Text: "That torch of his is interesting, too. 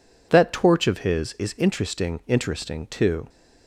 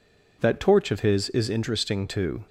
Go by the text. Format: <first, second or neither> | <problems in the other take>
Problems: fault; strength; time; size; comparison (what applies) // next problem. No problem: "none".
second | says "interesting" twice; at 2.2 s